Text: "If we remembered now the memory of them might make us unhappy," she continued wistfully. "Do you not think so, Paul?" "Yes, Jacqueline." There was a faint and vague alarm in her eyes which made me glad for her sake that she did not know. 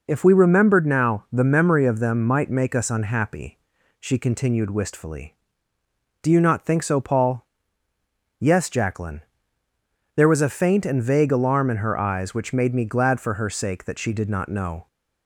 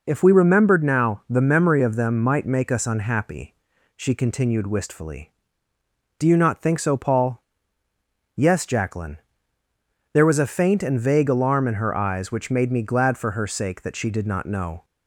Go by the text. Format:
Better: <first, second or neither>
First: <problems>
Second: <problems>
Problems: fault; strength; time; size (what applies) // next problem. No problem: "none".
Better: neither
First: none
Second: none